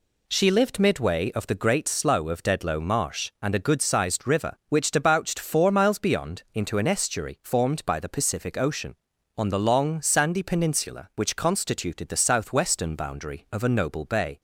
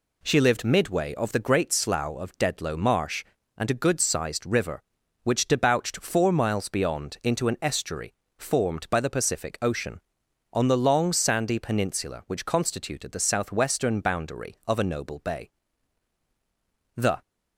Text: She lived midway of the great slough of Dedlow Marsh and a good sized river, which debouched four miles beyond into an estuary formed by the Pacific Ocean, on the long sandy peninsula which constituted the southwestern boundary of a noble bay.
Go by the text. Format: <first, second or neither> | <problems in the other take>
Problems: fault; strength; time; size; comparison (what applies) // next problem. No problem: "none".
first | pauses between "estuary" and "formed"; slight; at 8.1 s; 0.24 s long // goes on to say "The"; slight; from 16.9 s on; 0.26 s long